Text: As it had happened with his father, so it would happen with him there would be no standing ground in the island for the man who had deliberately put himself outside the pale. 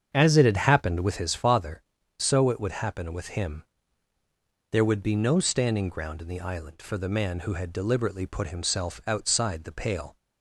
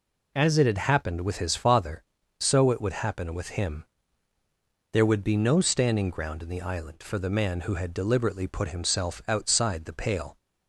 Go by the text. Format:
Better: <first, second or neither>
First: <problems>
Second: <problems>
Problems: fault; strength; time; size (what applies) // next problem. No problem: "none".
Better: second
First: starts louder than the rest; strong; until 1.2 s; 7.5 dB // pauses between "him" and "there"; at 3.6 s; 1.0 s long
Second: pauses between "him" and "there"; at 3.8 s; 1.0 s long